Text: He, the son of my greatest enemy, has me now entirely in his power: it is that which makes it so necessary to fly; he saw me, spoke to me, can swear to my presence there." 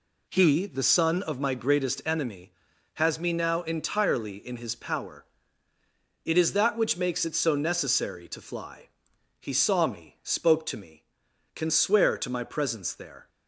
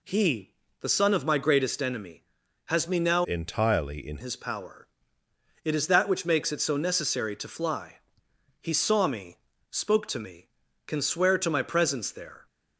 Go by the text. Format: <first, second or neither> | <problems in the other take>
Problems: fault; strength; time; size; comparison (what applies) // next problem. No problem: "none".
first | changes voice from "entirely" to "in"; from 3.2 to 4.1 s; 0.9 s long